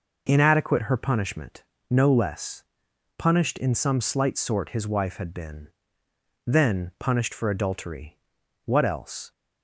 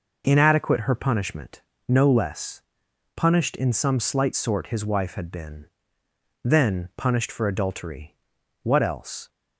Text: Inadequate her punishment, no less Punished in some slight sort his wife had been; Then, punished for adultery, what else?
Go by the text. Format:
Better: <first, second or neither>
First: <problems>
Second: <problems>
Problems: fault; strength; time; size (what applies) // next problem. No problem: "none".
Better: neither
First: pauses between "less" and "Punished"; noticeable; at 2.6 s; 0.54 s long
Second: pauses between "less" and "Punished"; noticeable; at 2.5 s; 0.54 s long